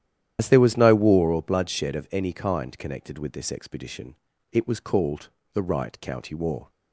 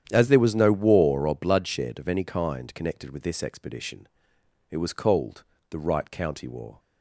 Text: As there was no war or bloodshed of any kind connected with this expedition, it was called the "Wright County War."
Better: second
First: loses the start of "As"; at 0.3 s; 80 ms // starts louder than the rest; strong; until 1.4 s; 11 dB // pauses between "called" and "the"; slight; at 5.2 s; 0.26 s long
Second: starts louder than the rest; strong; until 1.1 s; 9.5 dB // pauses between "called" and "the"; slight; at 5.4 s; 0.28 s long

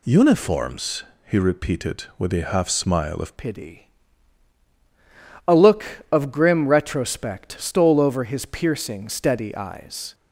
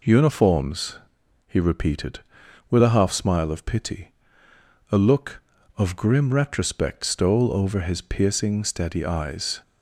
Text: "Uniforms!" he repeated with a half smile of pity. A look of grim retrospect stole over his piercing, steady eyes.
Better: second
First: changes voice at "pity"; from 3.3 s on; 6.8 s long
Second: none

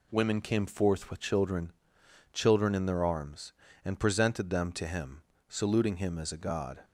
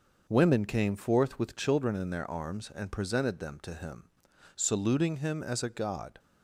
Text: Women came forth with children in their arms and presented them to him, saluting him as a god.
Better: second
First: says "children" twice; at 2.3 s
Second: none

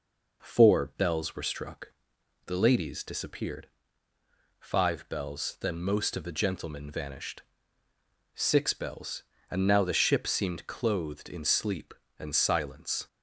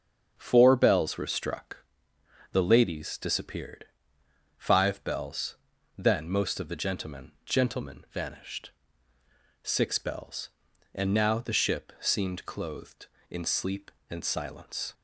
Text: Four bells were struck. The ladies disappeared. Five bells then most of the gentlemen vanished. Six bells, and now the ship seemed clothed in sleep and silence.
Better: first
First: none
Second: starts louder than the rest; strong; until 1.3 s; 7 dB // pauses between "bells" and "then"; at 5.5 s; 0.44 s long // says "gentlemen" twice; at 7.4 s

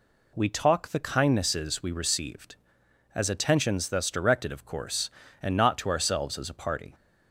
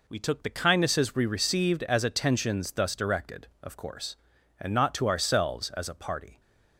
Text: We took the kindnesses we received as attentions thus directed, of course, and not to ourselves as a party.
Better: second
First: says "talk" for "took"; at 0.4 s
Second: none

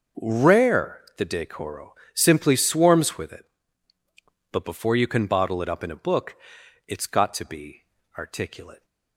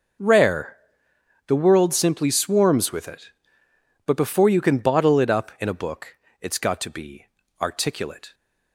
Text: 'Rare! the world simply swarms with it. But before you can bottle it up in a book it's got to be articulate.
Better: second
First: starts louder than the rest; noticeable; until 1.3 s; 6 dB // says "decoro" for "world"; at 1.2 s // pauses between "book" and "it's"; noticeable; at 6.3 s; 0.52 s long // pauses between "be" and "articulate"; slight; at 7.8 s; 0.34 s long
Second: pauses between "book" and "it's"; slight; at 6.1 s; 0.24 s long // pauses between "be" and "articulate"; slight; at 7.2 s; 0.34 s long

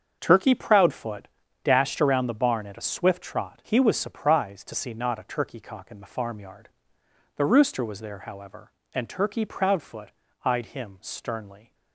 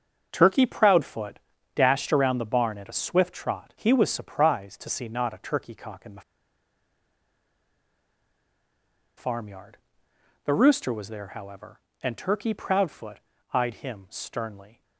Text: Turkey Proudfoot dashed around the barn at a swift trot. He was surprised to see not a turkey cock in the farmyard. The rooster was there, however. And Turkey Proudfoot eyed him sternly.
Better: first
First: starts louder than the rest; until 1.2 s; 7 dB // pauses between "Proudfoot" and "dashed"; slight; at 1.2 s; 0.34 s long // pauses between "Proudfoot" and "eyed"; slight; at 10.1 s; 0.30 s long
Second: starts louder than the rest; until 1.3 s; 7 dB // pauses between "Proudfoot" and "dashed"; slight; at 1.4 s; 0.34 s long // pauses between "the" and "farmyard"; strong; at 6.2 s; 2.9 s long // pauses between "Proudfoot" and "eyed"; slight; at 13.2 s; 0.30 s long

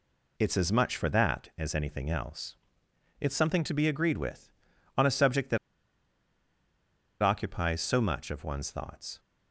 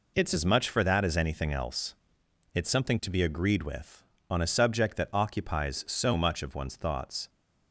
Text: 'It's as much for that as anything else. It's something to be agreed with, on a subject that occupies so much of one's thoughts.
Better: second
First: pauses between "that" and "occupies"; strong; at 5.5 s; 1.6 s long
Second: none

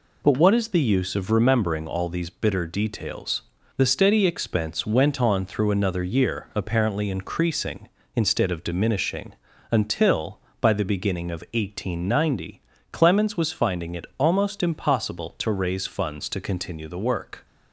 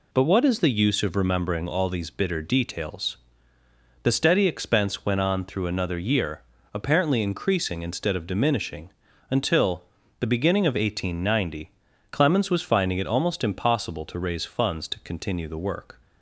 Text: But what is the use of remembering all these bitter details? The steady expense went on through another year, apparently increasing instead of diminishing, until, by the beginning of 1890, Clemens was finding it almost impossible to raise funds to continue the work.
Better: first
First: none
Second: skips "by"; at 10.0 s

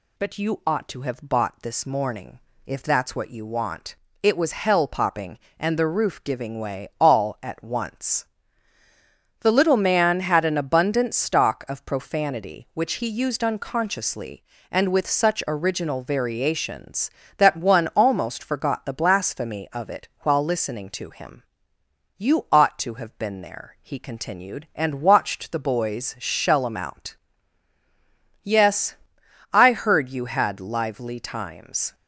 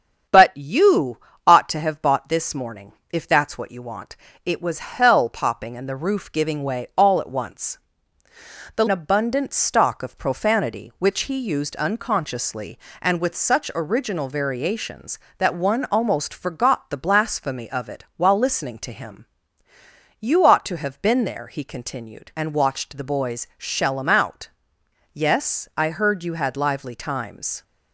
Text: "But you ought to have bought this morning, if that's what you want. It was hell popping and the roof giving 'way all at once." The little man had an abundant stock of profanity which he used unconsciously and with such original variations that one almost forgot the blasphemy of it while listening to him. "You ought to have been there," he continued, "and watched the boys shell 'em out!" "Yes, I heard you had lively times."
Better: first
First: none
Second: starts louder than the rest; strong; until 1.6 s; 8 dB // pauses between "you" and "ought"; slight; at 1.1 s; 0.28 s long // skips "little man had an"; at 8.8 s

